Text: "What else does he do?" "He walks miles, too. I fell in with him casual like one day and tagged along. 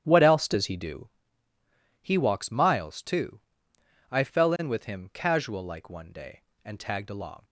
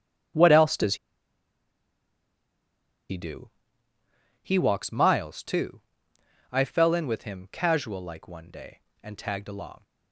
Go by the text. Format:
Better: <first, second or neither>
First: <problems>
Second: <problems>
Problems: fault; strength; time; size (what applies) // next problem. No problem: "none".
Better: first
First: starts louder than the rest; strong; until 1.0 s; 10.5 dB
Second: starts louder than the rest; strong; until 4.4 s; 10.5 dB // pauses between "does" and "he"; strong; at 0.9 s; 2.1 s long